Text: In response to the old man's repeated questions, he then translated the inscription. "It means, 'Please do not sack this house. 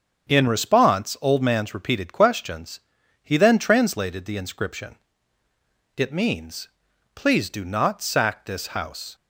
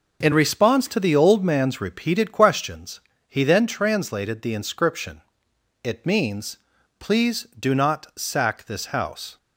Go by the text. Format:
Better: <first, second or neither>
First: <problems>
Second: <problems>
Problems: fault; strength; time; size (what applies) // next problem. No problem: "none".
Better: second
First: starts louder than the rest; strong; until 1.3 s; 7.5 dB // skips "to the"; at 1.1 s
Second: none